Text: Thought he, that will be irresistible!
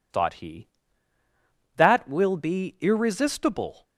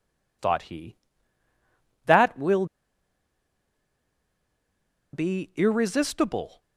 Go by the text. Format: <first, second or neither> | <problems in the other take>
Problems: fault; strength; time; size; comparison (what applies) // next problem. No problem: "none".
first | pauses between "will" and "be"; strong; at 2.6 s; 2.4 s long